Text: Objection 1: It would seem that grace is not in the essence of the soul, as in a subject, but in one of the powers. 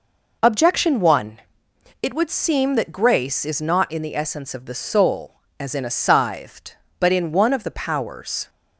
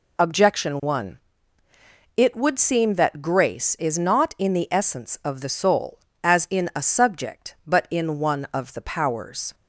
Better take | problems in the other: second | says "scythed" for "subject"; at 5.8 s

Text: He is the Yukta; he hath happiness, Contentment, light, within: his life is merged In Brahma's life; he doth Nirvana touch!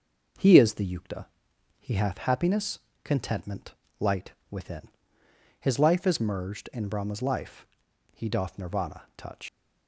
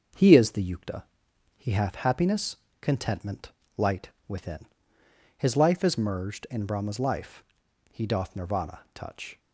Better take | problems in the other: second | starts louder than the rest; noticeable; until 1.9 s; 6 dB; also in the second // leaves "touch" unfinished; at 9.4 s; 130 ms

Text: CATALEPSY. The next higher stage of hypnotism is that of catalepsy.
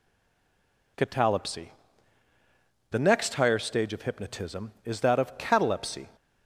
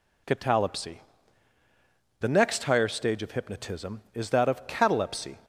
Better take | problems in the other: second | stays silent before the first word; slight; until 0.9 s; 0.9 s long

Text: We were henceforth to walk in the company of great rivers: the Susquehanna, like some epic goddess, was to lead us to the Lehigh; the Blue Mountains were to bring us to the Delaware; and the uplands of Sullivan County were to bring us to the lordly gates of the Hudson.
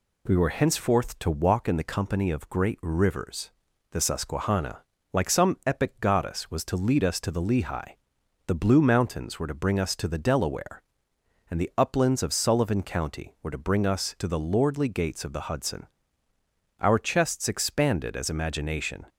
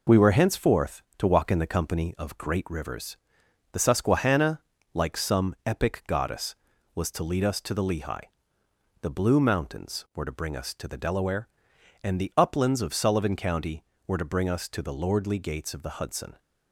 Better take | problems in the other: second | goes on to say "Our chests expanded as imagination"; strong; from 16.8 s on; 2.2 s long

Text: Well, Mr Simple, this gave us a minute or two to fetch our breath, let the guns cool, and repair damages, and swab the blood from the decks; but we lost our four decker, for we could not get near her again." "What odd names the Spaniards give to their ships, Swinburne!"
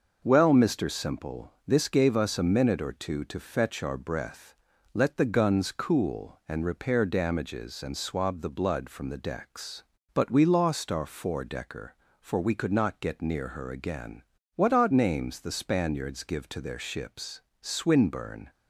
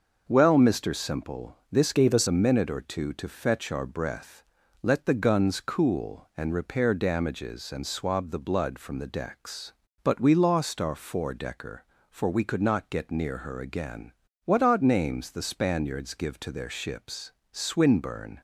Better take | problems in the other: first | starts louder than the rest; noticeable; until 1.2 s; 6 dB; noticeable in the first // changes voice from "gave" to "us"; from 1.9 to 2.2 s; 0.3 s long

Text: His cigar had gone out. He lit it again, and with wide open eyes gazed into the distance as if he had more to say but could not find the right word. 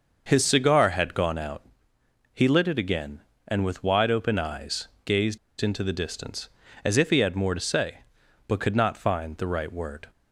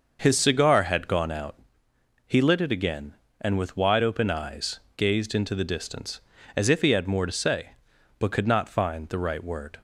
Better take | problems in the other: second | starts louder than the rest; noticeable; until 1.2 s; 6 dB; noticeable in the second // pauses between "eyes" and "gazed"; slight; at 4.8 s; 0.16 s long; slight in the second // pauses between "gazed" and "into"; slight; at 5.3 s; 0.23 s long

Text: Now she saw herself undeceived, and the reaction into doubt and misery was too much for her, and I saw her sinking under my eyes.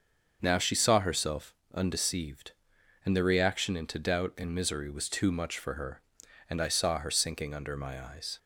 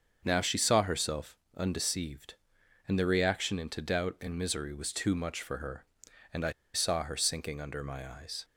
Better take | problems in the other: first | starts louder than the rest; until 1.2 s; 6.5 dB; also in the first // pauses between "herself" and "undeceived"; slight; at 1.3 s; 0.22 s long; slight in the first // pauses between "I" and "saw"; slight; at 6.5 s; 0.21 s long

